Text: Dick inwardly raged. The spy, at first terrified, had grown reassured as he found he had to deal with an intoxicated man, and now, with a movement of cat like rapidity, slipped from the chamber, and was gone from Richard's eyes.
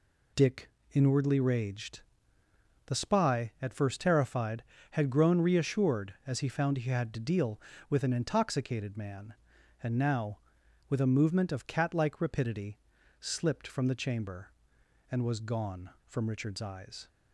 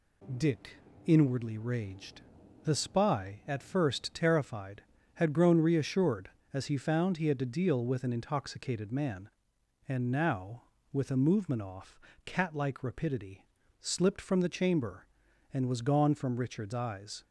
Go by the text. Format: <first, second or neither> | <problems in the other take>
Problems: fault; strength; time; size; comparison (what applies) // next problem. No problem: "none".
first | pauses between "Dick" and "inwardly"; slight; at 0.7 s; 0.30 s long; slight in the first // says "off" for "of"; at 11.6 s